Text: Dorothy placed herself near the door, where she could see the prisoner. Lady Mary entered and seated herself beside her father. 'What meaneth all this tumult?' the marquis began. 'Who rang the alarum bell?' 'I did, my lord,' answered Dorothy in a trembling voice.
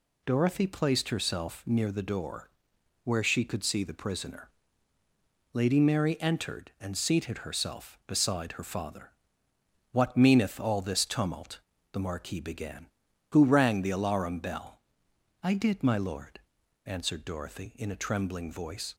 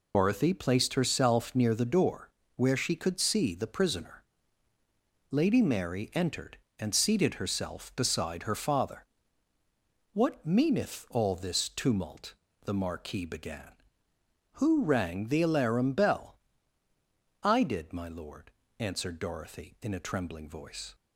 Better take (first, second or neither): first